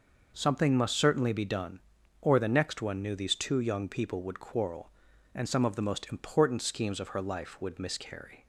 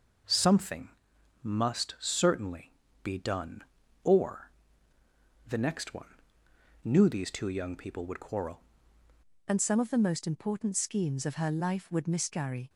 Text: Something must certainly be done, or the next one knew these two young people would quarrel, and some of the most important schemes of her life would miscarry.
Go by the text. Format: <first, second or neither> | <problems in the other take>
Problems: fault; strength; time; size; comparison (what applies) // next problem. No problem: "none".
first | pauses between "Something" and "must"; noticeable; at 0.8 s; 0.54 s long // pauses between "certainly" and "be"; slight; at 2.7 s; 0.32 s long // pauses between "or" and "the"; noticeable; at 4.5 s; 0.94 s long // pauses between "one" and "knew"; noticeable; at 6.1 s; 0.68 s long // changes voice at "and"; from 9.4 s on; 3.2 s long